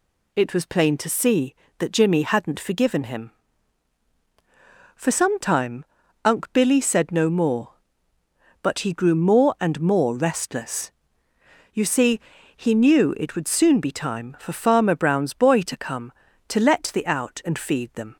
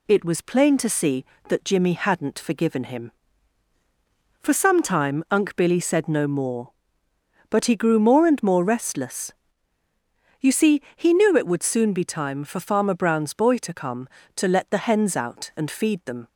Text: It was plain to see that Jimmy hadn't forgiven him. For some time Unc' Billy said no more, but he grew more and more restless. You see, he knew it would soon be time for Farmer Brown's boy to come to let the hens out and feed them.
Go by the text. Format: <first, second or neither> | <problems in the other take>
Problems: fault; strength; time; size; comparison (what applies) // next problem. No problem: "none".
second | pauses between "time" and "Unc"; at 5.8 s; 0.40 s long // skips "hens"; at 17.0 s